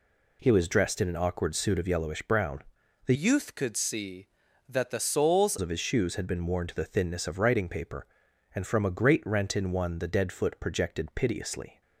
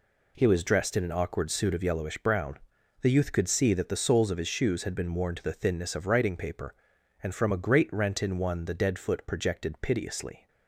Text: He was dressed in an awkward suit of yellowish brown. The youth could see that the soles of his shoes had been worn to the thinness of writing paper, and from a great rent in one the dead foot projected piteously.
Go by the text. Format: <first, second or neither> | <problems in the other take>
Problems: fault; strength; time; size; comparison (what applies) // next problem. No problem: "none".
second | changes voice from "youth" to "soles"; from 3.1 to 5.5 s; 2.4 s long